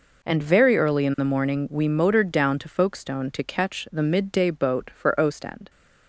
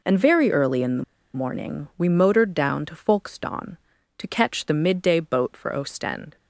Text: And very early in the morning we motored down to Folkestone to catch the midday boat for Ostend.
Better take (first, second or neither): first